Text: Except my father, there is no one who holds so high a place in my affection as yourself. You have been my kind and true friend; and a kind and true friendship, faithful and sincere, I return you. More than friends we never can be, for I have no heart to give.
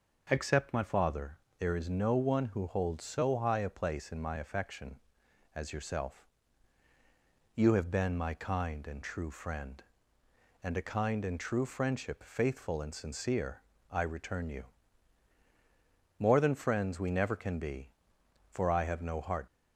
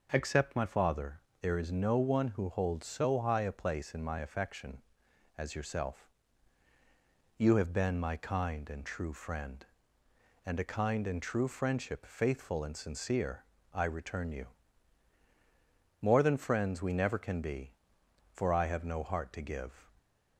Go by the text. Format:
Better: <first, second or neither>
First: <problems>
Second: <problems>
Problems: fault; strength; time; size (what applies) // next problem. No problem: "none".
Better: second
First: stops before "to give"; at 19.4 s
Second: none